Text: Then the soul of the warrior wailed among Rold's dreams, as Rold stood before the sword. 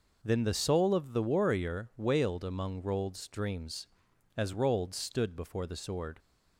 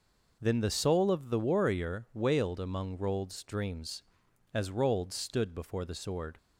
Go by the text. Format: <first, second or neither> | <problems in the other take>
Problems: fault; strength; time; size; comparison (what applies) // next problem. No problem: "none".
neither | none